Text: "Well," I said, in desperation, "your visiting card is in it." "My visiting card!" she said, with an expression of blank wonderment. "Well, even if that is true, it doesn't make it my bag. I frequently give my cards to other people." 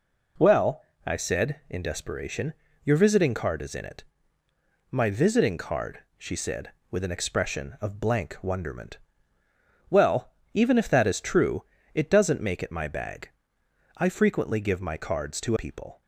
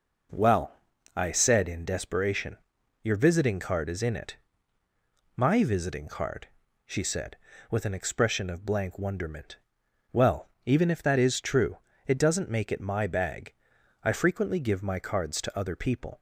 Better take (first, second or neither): second